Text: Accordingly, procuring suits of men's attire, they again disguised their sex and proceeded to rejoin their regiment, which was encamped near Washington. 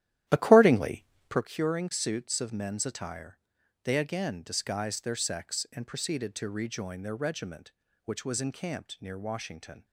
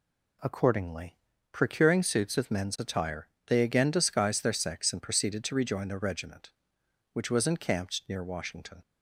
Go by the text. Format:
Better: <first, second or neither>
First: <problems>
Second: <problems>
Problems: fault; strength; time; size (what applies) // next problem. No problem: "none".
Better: second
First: starts louder than the rest; strong; until 1.4 s; 12.5 dB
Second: none